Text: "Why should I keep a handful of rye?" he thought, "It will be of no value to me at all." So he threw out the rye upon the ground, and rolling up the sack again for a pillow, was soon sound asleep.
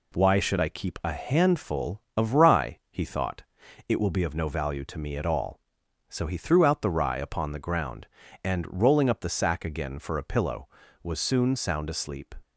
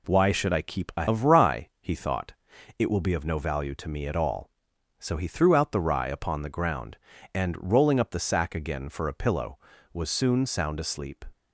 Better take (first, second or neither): first